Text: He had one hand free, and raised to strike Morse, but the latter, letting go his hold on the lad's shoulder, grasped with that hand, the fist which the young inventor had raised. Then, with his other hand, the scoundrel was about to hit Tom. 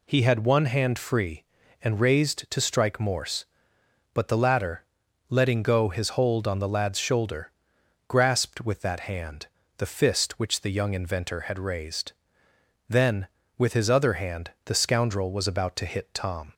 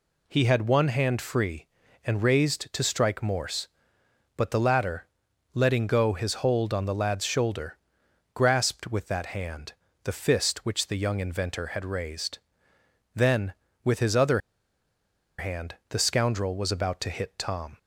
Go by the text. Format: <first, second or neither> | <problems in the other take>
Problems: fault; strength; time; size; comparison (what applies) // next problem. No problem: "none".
first | pauses between "other" and "hand"; at 14.3 s; 0.98 s long